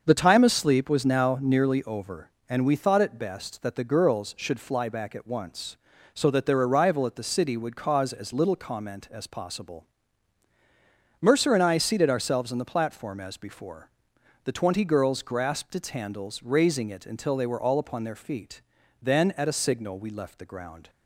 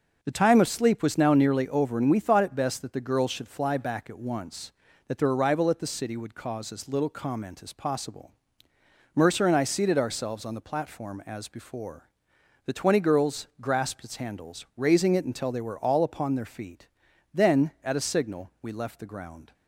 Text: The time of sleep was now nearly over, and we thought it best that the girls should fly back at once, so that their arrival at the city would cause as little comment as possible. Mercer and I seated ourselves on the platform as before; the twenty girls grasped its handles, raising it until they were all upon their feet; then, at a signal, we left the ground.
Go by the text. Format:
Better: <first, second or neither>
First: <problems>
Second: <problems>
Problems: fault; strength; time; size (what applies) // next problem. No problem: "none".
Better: first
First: starts louder than the rest; until 1.0 s; 6.5 dB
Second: starts louder than the rest; until 1.2 s; 6.5 dB // skips "so"; at 4.8 s